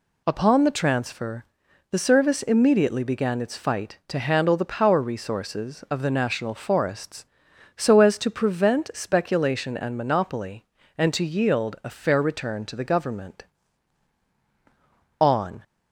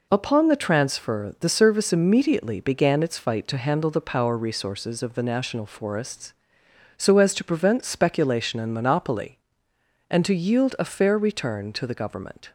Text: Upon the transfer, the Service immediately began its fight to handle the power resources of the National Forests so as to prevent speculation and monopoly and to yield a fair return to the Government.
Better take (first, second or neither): second